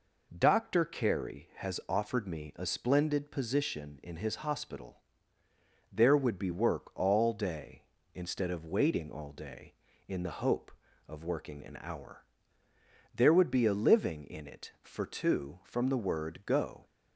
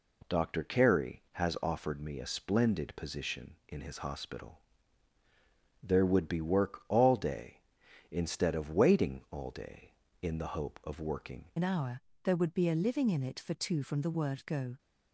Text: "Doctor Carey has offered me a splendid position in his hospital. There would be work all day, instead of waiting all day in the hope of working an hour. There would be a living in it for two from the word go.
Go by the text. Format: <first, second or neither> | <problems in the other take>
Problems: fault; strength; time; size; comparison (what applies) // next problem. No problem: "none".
first | changes voice at "an"; from 11.5 s on; 3.2 s long